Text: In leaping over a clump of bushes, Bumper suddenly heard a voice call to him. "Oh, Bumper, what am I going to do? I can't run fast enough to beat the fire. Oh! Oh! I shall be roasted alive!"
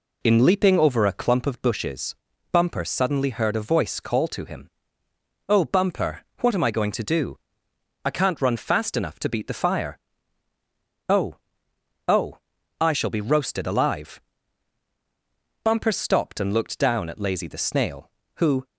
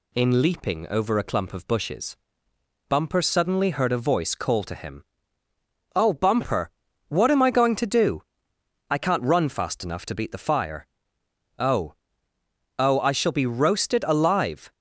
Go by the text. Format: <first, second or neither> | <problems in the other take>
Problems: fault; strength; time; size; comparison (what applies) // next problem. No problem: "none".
second | goes on to say "Bumper stopped and looked down at Lazy the Snail who"; strong; from 15.6 s on; 3.0 s long